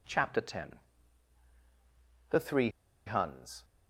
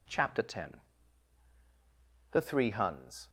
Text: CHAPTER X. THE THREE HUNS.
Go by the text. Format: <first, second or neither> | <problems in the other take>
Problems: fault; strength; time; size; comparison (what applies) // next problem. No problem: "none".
second | pauses between "THREE" and "HUNS"; at 2.6 s; 0.37 s long